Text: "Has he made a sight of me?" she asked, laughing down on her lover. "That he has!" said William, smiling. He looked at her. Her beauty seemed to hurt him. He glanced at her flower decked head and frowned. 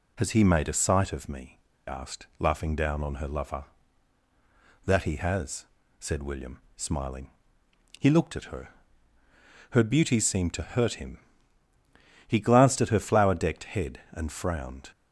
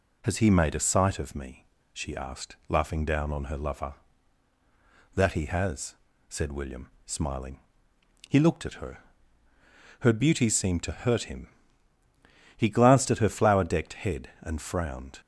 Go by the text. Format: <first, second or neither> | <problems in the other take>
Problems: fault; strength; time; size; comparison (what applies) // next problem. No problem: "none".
second | skips "she"; at 1.7 s